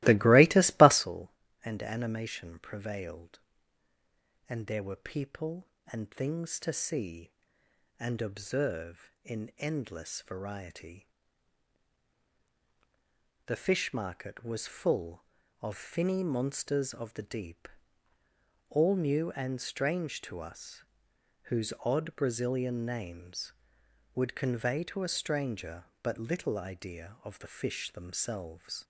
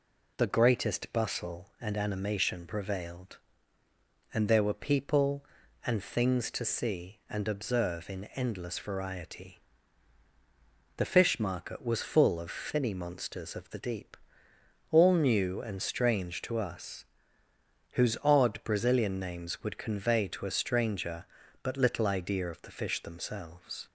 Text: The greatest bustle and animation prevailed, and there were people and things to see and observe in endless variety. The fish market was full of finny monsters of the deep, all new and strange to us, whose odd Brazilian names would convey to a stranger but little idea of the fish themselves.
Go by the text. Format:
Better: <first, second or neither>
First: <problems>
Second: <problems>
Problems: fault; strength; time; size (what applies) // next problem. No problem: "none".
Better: second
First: starts louder than the rest; strong; until 1.0 s; 18 dB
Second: none